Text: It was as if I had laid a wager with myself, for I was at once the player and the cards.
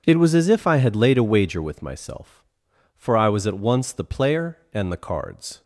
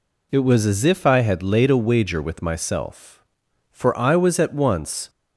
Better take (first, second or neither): first